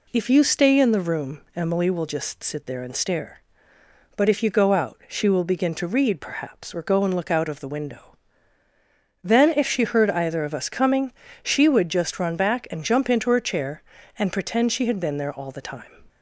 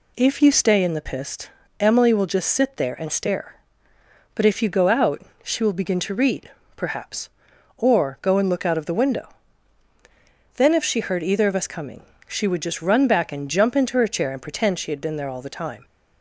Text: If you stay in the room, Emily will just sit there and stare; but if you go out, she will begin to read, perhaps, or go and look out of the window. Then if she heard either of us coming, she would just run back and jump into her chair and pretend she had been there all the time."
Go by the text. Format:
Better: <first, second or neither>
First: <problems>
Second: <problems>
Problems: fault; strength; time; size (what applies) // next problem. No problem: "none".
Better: first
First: none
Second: says "pist" for "room"; at 1.0 s